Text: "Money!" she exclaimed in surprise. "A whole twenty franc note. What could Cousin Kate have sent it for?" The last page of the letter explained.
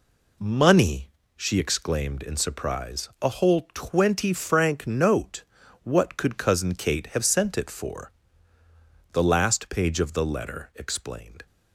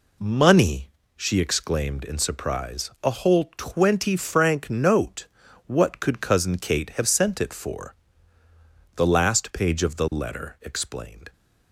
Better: neither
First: none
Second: none

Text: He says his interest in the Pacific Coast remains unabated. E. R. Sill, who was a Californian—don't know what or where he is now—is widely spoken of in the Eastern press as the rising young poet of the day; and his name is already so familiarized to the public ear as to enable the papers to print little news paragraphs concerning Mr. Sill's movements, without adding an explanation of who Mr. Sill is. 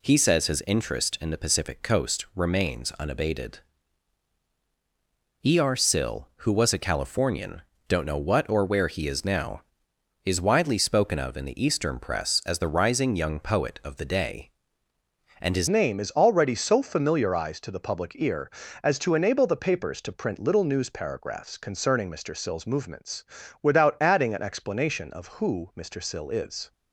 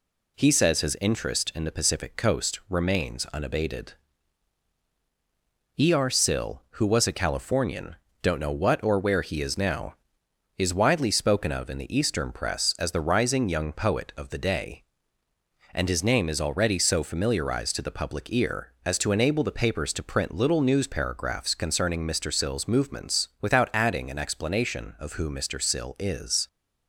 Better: second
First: changes voice at "name"; from 15.6 s on; 11.1 s long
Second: none

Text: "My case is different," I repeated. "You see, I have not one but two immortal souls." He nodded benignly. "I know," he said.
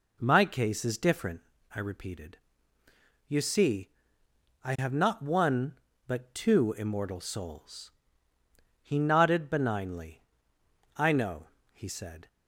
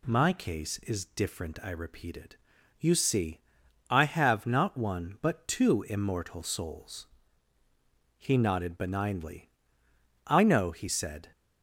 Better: neither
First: none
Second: none

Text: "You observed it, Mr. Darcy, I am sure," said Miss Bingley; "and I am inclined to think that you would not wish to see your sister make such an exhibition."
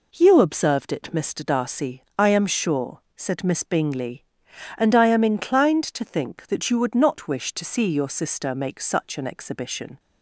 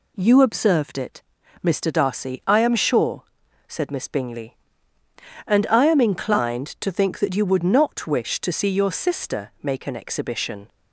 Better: first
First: none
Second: skips "such"; at 9.8 s

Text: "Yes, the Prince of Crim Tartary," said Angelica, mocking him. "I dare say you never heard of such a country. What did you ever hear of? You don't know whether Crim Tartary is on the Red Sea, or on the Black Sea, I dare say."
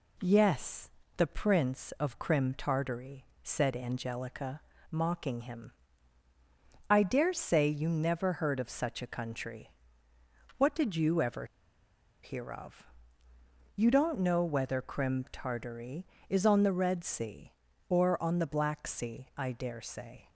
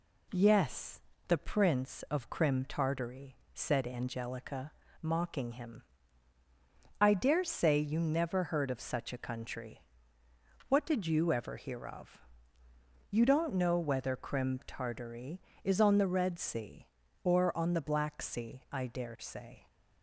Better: second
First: pauses between "ever" and "hear"; noticeable; at 11.4 s; 0.79 s long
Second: none

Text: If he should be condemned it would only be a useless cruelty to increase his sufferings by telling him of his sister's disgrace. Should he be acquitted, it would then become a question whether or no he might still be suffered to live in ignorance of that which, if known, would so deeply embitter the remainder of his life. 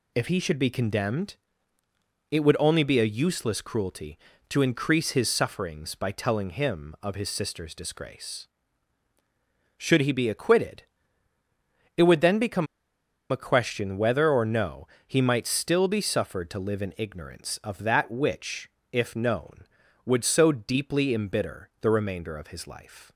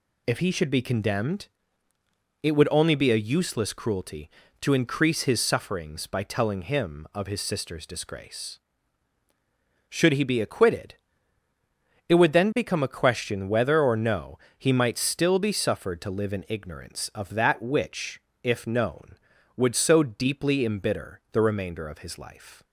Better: second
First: pauses between "condemned" and "it"; noticeable; at 1.3 s; 0.96 s long // pauses between "become" and "a"; noticeable; at 12.6 s; 0.64 s long // pauses between "no" and "he"; slight; at 14.8 s; 0.20 s long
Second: pauses between "condemned" and "it"; noticeable; at 1.4 s; 0.96 s long // pauses between "no" and "he"; slight; at 14.3 s; 0.20 s long

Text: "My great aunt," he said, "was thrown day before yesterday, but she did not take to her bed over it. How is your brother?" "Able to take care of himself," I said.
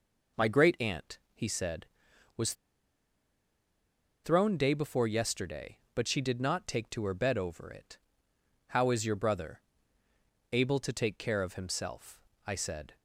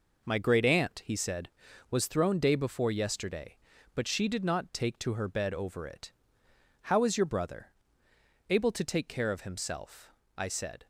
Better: second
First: pauses between "was" and "thrown"; strong; at 2.5 s; 1.7 s long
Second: none

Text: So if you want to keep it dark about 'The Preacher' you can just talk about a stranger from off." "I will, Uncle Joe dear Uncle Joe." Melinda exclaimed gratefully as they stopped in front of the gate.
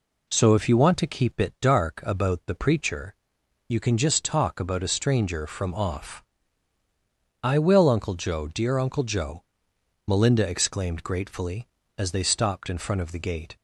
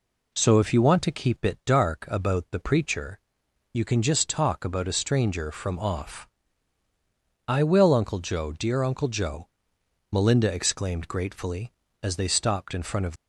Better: first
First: pauses between "Preacher" and "you"; noticeable; at 3.1 s; 0.56 s long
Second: pauses between "Preacher" and "you"; noticeable; at 3.1 s; 0.56 s long // stops before "the gate"; at 13.1 s

